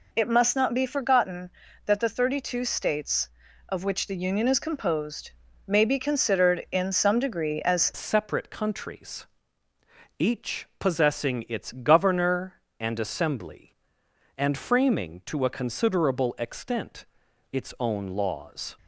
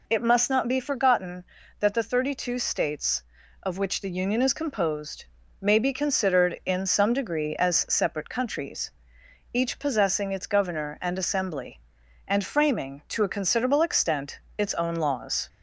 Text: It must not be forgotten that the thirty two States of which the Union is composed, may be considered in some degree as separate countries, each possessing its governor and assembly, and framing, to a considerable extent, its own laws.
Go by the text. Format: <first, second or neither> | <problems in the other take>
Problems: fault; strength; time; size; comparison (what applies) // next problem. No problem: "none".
second | changes voice at "separate"; from 7.9 s on; 10.8 s long